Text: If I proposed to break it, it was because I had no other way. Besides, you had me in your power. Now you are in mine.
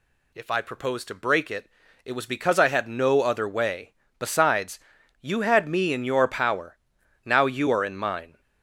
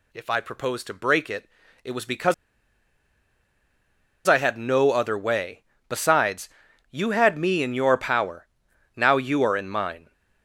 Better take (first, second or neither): first